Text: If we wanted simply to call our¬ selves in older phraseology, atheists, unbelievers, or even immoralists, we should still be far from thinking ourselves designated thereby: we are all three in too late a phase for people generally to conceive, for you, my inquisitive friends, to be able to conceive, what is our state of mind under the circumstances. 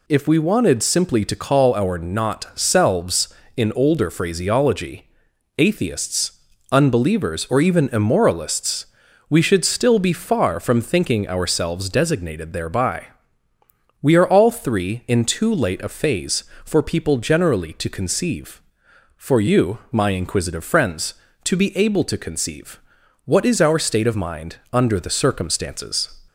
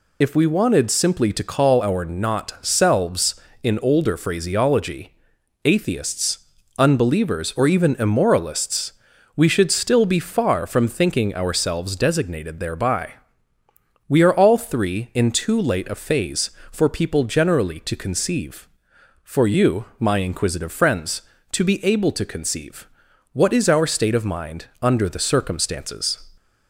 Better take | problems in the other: first | loses the start of "If"; at 0.2 s; 45 ms // pauses between "mind" and "under"; slight; at 24.6 s; 0.16 s long; slight in the first

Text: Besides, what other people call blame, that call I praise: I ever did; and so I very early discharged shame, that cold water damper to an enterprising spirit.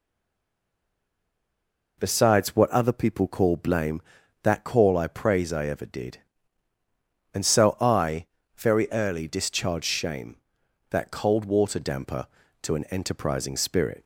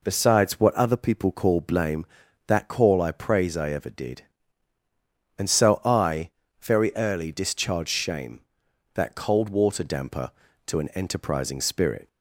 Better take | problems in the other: second | stays silent before the first word; noticeable; until 1.9 s; 1.9 s long // pauses between "I" and "very"; slight; at 8.2 s; 0.30 s long; slight in the second

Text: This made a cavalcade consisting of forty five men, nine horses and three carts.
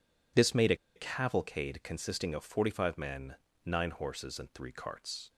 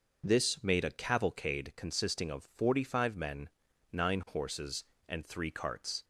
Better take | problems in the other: second | pauses between "a" and "cavalcade"; slight; at 0.7 s; 0.20 s long

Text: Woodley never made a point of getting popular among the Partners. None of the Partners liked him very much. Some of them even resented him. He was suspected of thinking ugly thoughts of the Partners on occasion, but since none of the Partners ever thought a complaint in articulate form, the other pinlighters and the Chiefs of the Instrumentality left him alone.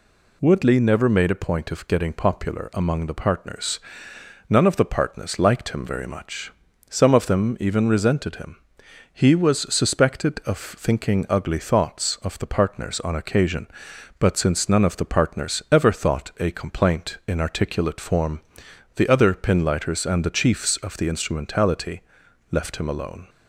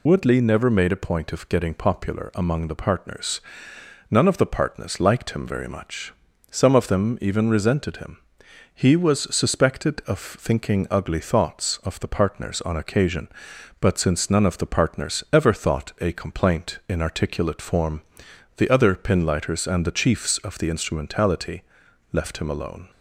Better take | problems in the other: first | loses the start of "Woodley"; at 0.0 s; 35 ms // pauses between "Instrumentality" and "left"; noticeable; at 21.6 s; 0.50 s long; noticeable in the first

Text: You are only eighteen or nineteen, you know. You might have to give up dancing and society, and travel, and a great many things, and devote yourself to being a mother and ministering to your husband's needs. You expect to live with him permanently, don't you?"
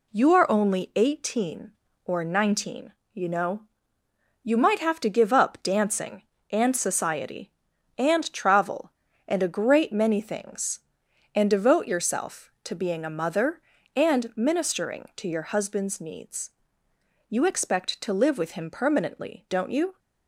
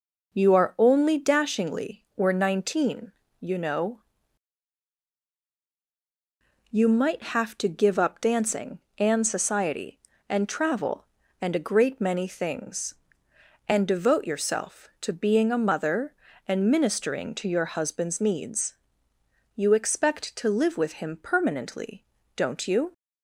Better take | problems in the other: first | says "dashingly" for "eighteen"; at 1.1 s

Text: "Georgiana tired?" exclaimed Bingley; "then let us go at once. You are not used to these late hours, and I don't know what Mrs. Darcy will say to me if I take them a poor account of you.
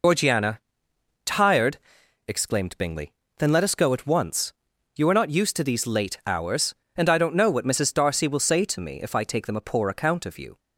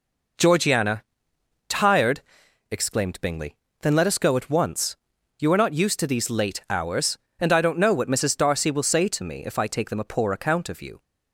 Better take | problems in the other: second | loses the start of "Georgiana"; at 0.0 s; 100 ms // pauses between "Georgiana" and "tired"; noticeable; at 0.6 s; 0.64 s long; noticeable in the second

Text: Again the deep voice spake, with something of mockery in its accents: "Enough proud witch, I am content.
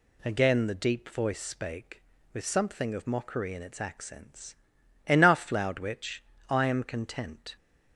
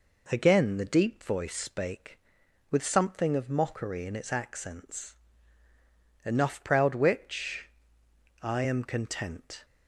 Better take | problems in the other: second | says "loud" for "proud"; at 5.4 s

